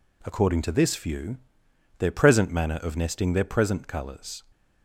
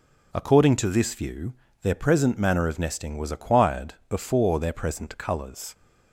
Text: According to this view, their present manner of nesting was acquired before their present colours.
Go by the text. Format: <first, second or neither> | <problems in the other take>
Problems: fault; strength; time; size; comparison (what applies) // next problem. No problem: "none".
second | skips "was acquired before"; at 3.3 s